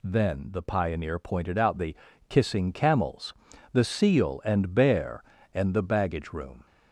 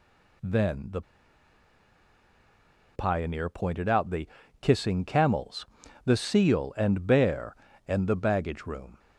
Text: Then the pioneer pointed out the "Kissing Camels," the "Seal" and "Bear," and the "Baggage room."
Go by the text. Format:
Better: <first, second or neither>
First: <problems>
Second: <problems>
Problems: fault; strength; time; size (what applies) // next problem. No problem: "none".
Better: first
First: pauses between "the" and "Kissing"; slight; at 1.9 s; 0.32 s long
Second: pauses between "the" and "pioneer"; strong; at 1.0 s; 1.9 s long // pauses between "the" and "Kissing"; slight; at 4.2 s; 0.32 s long